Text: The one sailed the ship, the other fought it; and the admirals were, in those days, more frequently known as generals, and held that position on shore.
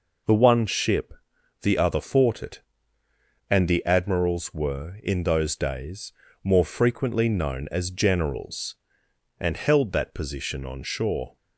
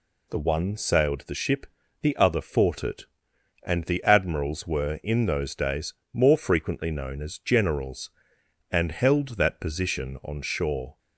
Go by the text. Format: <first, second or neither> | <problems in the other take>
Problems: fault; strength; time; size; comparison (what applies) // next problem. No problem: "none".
second | skips "sailed the"; at 0.6 s